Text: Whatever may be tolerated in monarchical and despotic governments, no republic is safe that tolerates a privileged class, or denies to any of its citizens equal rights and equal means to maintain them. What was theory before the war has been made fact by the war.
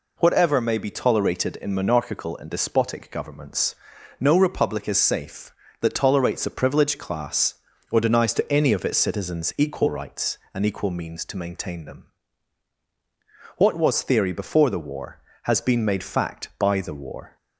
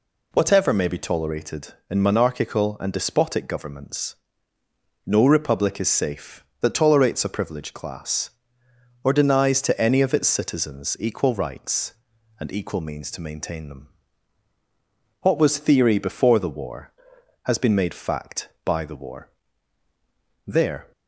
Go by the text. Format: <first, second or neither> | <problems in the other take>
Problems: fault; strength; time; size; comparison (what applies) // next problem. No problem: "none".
first | goes on to say "There"; slight; from 20.4 s on; 0.44 s long